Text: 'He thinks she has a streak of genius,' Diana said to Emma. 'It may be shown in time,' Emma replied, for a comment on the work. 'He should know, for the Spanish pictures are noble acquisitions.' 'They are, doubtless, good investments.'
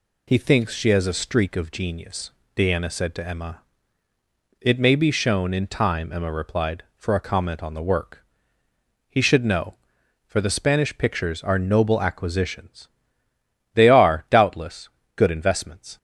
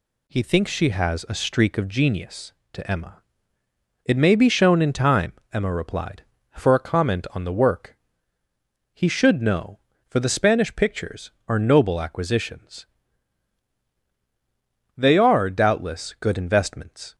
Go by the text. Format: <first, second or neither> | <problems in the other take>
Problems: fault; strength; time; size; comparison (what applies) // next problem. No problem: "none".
first | skips "Diana said"; at 2.6 s